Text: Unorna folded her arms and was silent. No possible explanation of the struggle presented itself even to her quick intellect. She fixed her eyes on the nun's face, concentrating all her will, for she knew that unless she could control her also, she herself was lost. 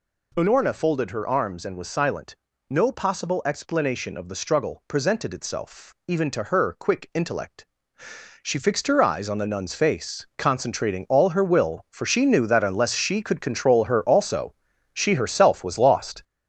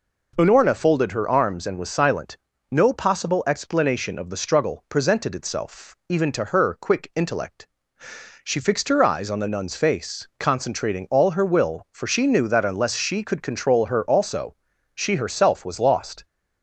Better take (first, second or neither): second